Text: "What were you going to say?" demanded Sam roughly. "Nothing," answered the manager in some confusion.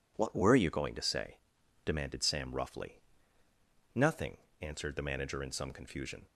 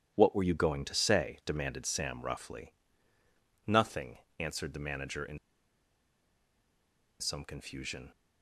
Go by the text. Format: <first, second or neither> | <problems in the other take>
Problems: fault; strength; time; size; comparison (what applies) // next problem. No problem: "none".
first | starts louder than the rest; strong; until 1.1 s; 10.5 dB // pauses between "in" and "some"; strong; at 5.3 s; 1.8 s long